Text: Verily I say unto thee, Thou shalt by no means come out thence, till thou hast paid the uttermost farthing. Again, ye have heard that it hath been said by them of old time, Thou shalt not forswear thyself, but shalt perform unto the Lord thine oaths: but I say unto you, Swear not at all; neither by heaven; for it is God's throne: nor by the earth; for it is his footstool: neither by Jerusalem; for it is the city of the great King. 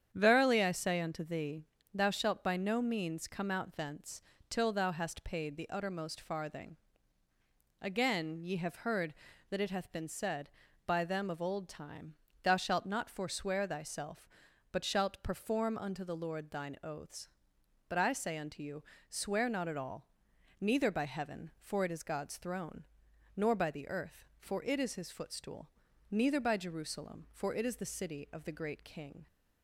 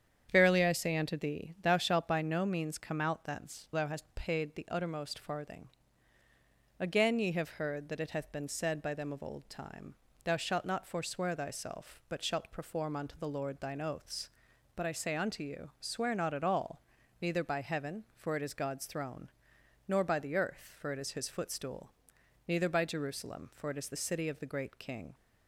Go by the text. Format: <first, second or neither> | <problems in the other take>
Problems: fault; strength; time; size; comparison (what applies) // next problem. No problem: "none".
first | starts louder than the rest; strong; until 1.3 s; 8.5 dB; strong in the first // skips "till"; at 3.6 s